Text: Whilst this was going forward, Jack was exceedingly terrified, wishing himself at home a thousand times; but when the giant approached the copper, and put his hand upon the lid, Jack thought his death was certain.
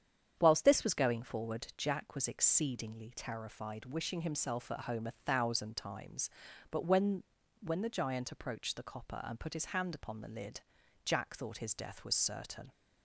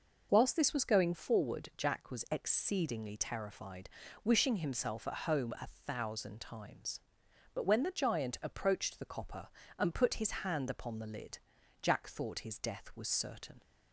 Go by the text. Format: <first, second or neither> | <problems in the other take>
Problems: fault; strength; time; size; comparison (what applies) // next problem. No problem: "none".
second | starts louder than the rest; strong; until 1.3 s; 8.5 dB // says "when" twice; at 7.6 s